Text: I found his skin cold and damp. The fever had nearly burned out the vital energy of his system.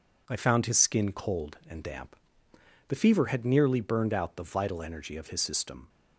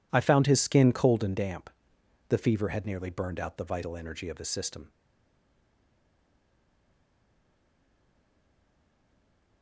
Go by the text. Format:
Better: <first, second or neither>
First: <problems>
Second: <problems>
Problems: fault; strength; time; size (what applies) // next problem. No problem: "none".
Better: first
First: none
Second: stays silent after the last word; strong; from 4.8 s on; 4.8 s long